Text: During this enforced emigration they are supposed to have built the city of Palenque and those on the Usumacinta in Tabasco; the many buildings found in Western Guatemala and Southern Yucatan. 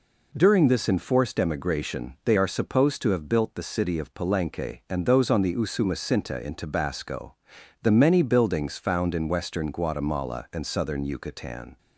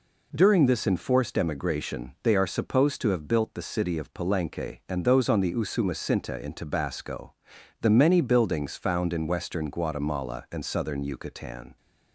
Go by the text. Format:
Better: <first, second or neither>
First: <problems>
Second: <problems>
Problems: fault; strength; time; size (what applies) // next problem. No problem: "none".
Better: neither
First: none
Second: none